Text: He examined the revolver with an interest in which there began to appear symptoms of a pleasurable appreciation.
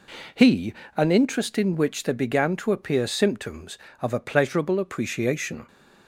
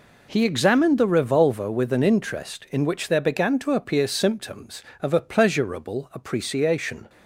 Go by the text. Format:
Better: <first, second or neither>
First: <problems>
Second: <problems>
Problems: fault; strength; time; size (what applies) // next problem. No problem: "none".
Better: second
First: skips "examined the revolver with"; at 0.8 s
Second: none